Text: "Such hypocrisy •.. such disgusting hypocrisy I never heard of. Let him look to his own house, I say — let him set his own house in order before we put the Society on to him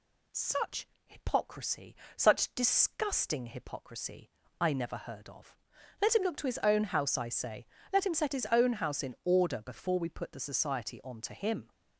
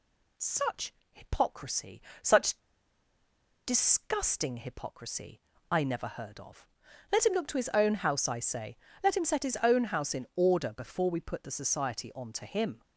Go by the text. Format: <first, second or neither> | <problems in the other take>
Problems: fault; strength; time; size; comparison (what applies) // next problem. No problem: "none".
first | pauses between "Such" and "hypocrisy"; slight; at 0.9 s; 0.18 s long; slight in the first // pauses between "such" and "disgusting"; at 2.5 s; 1.0 s long // pauses between "hypocrisy" and "I"; slight; at 5.4 s; 0.30 s long; slight in the first